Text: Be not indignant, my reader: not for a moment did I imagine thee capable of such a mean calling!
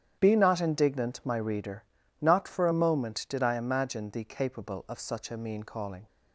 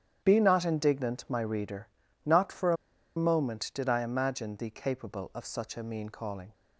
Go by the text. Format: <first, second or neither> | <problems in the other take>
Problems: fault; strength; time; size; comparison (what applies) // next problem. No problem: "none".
first | starts louder than the rest; strong; until 1.2 s; 9.5 dB; strong in the first // pauses between "a" and "moment"; at 2.7 s; 0.40 s long